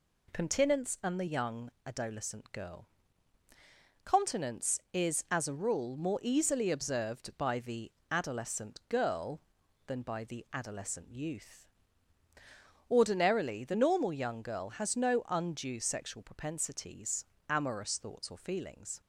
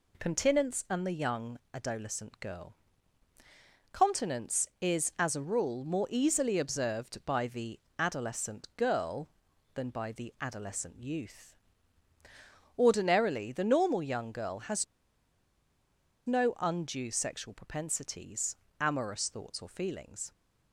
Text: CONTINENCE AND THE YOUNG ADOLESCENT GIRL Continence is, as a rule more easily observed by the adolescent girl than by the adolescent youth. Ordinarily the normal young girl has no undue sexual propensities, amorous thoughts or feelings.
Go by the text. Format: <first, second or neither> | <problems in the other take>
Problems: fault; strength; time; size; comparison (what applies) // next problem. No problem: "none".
first | pauses between "YOUNG" and "ADOLESCENT"; slight; at 1.5 s; 0.16 s long; slight in the first // pauses between "GIRL" and "Continence"; at 2.7 s; 1.1 s long; also in the first // pauses between "the" and "adolescent"; slight; at 7.7 s; 0.20 s long; slight in the first // pauses between "has" and "no"; strong; at 14.8 s; 1.4 s long